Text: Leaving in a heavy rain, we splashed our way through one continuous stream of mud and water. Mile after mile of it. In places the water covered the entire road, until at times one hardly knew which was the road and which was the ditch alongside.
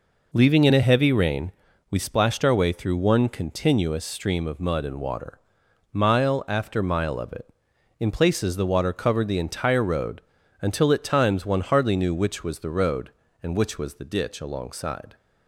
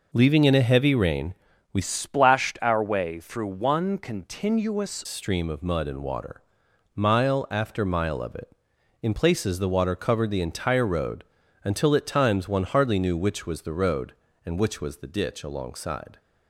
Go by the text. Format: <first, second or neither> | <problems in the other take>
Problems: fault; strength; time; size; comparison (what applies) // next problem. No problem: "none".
first | changes voice from "splashed" to "continuous"; from 1.8 to 5.0 s; 3.2 s long